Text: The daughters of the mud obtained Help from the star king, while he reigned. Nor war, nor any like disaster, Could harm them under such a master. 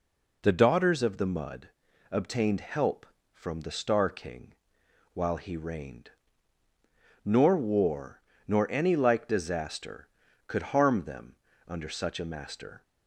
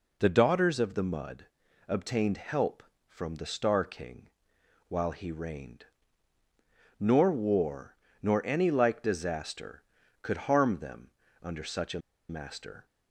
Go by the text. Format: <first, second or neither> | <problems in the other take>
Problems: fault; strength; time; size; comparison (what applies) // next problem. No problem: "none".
first | pauses between "mud" and "obtained"; at 1.4 s; 0.42 s long; also in the first // pauses between "them" and "under"; slight; at 11.0 s; 0.34 s long; slight in the first // pauses between "a" and "master"; slight; at 11.9 s; 0.30 s long